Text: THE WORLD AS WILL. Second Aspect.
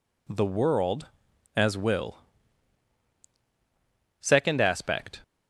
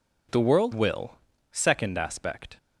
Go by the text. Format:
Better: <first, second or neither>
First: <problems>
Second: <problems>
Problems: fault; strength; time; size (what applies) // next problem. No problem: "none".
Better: first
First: none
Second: skips "AS"; at 0.7 s